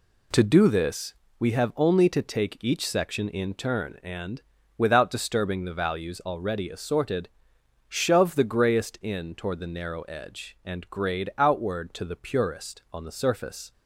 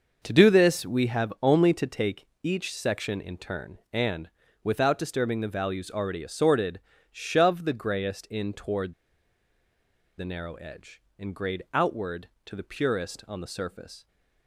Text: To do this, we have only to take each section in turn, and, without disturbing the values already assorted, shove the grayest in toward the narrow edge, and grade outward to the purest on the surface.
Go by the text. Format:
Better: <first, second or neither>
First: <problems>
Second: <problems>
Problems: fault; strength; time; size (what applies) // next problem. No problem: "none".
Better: first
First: none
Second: pauses between "take" and "each"; slight; at 2.2 s; 0.18 s long // pauses between "toward" and "the"; strong; at 8.9 s; 1.2 s long